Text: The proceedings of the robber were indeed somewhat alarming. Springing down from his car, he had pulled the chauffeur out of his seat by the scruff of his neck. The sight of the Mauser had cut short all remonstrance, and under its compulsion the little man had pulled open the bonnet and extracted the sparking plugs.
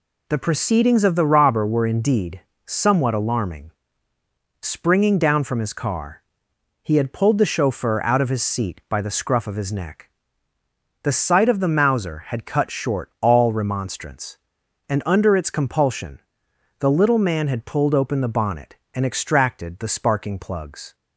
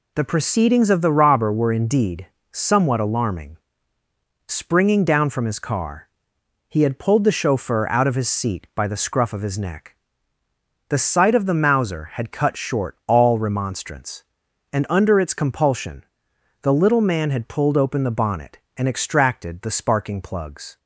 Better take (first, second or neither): neither